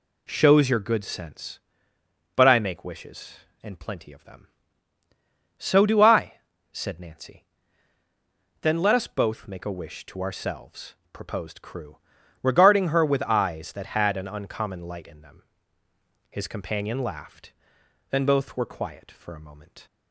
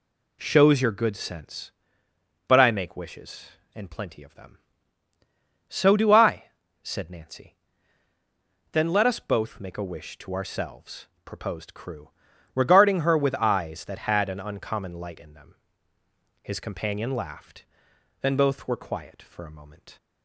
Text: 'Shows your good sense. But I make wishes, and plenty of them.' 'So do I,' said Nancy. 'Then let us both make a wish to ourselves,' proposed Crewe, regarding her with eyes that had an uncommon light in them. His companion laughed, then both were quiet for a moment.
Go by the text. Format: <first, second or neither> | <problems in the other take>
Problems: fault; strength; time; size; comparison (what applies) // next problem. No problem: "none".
neither | none